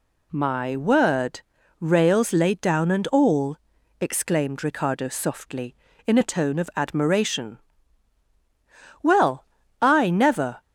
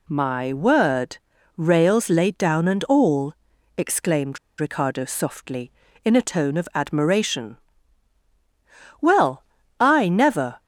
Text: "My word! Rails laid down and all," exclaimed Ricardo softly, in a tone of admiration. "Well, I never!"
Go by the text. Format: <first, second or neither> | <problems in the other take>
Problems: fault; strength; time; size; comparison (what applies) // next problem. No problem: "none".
first | pauses between "exclaimed" and "Ricardo"; slight; at 4.3 s; 0.20 s long